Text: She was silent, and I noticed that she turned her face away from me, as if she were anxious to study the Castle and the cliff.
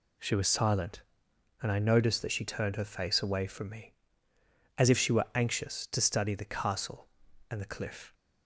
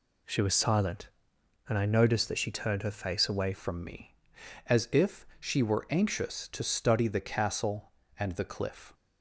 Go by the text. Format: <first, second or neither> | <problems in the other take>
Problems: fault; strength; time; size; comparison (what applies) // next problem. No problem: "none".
first | changes voice at "from"; from 3.5 s on; 5.4 s long